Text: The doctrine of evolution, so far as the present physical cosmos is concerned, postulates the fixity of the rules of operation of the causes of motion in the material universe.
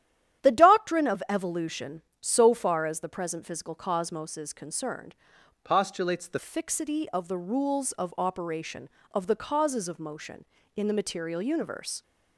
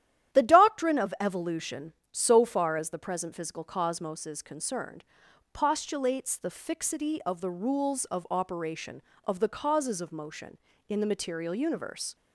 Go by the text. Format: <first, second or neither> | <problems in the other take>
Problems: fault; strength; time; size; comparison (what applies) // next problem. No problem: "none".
second | starts louder than the rest; strong; until 1.4 s; 11 dB; strong in the second // changes voice from "postulates" to "the"; from 5.6 to 6.3 s; 0.7 s long